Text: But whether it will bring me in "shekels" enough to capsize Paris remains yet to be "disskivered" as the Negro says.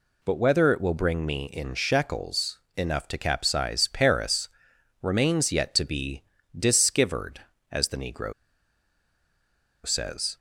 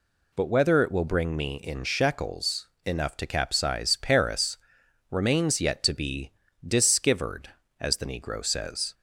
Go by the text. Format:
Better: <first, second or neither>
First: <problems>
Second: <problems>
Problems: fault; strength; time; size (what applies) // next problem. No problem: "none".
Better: second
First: pauses between "shekels" and "enough"; slight; at 2.5 s; 0.18 s long // pauses between "Paris" and "remains"; noticeable; at 4.4 s; 0.54 s long // pauses between "be" and "disskivered"; slight; at 6.2 s; 0.34 s long // pauses between "Negro" and "says"; strong; at 8.3 s; 1.5 s long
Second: pauses between "shekels" and "enough"; slight; at 2.6 s; 0.18 s long // pauses between "Paris" and "remains"; noticeable; at 4.5 s; 0.54 s long // pauses between "be" and "disskivered"; slight; at 6.3 s; 0.34 s long